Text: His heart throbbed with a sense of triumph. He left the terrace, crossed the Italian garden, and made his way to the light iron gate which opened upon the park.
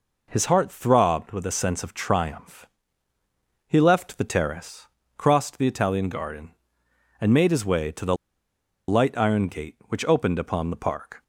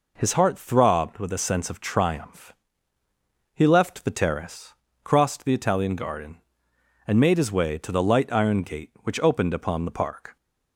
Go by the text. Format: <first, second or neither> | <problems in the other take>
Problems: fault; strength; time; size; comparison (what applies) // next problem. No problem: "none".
second | pauses between "the" and "light"; noticeable; at 8.1 s; 0.73 s long